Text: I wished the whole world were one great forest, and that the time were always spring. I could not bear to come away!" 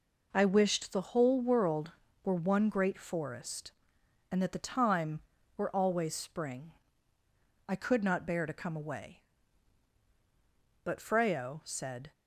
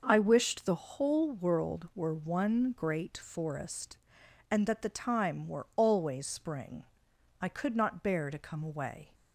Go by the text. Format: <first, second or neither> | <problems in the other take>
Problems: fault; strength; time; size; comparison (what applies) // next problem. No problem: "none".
second | goes on to say "But Freyo said"; noticeable; from 10.8 s on; 1.2 s long